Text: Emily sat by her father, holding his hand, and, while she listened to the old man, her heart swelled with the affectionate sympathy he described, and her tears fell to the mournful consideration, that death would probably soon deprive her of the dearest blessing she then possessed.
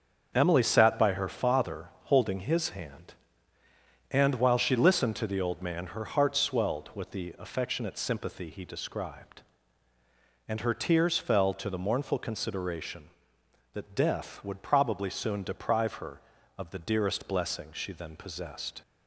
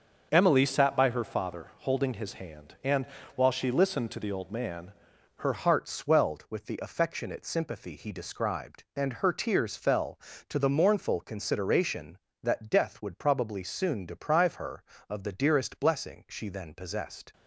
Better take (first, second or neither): first